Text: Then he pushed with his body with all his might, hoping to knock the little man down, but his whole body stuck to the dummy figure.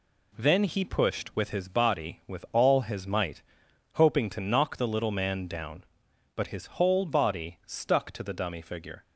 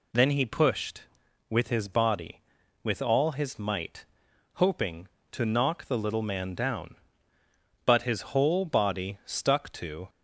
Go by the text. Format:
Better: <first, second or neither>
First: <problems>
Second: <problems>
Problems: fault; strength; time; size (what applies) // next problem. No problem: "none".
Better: first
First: none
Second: stops before "the dummy figure"; at 10.0 s